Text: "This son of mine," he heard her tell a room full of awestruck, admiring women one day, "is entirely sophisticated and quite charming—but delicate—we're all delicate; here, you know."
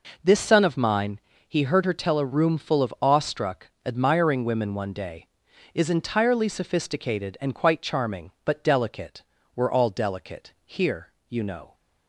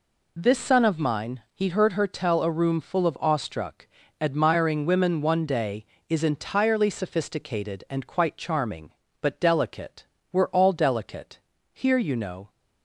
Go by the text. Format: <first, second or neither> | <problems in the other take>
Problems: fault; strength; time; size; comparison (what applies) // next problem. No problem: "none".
neither | none